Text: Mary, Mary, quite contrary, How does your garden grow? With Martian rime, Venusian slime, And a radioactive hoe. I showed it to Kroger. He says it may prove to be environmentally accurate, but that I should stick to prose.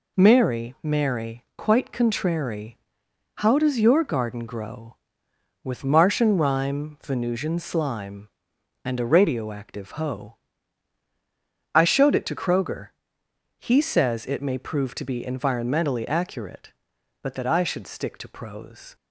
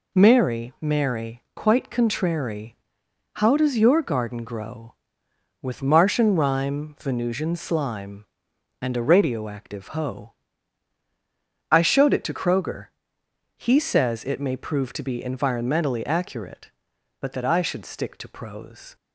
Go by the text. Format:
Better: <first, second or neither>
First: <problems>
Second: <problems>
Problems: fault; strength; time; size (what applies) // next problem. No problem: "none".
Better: neither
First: none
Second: none